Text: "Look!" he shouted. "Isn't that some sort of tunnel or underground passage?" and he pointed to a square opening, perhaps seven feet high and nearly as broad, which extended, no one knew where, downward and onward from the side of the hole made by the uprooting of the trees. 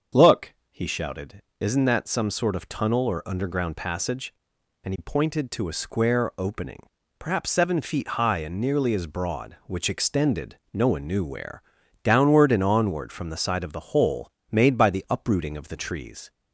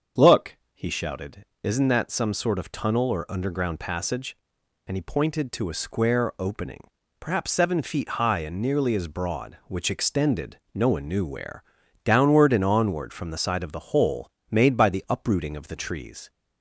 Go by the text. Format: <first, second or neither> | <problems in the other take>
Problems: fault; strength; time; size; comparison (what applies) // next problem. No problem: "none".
neither | starts louder than the rest; the same in both // pauses between "hole" and "made"; slight; the same in both